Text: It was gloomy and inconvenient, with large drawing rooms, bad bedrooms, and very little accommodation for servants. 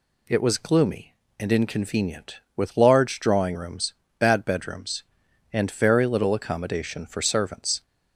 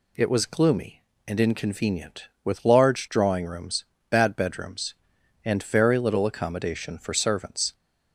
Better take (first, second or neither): neither